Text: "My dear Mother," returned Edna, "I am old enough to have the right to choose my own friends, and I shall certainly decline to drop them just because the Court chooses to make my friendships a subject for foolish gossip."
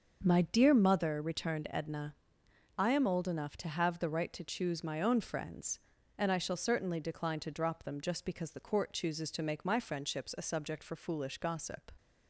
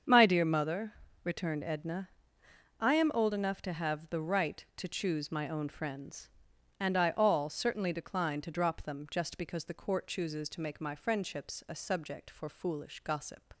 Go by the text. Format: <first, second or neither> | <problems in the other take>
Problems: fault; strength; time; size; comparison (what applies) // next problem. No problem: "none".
first | starts louder than the rest; strong; until 1.3 s; 7 dB; also in the first // says "all" for "shall"; at 7.1 s